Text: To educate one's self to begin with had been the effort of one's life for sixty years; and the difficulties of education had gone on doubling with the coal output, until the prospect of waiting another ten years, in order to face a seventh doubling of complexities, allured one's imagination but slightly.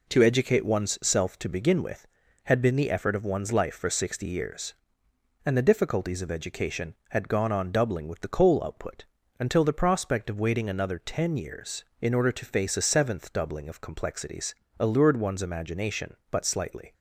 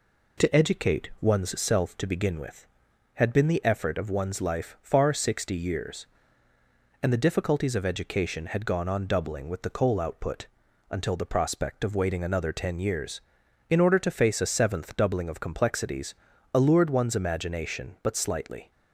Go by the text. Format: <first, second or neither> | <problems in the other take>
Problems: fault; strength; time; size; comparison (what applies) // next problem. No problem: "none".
first | says "far" for "for"; at 4.8 s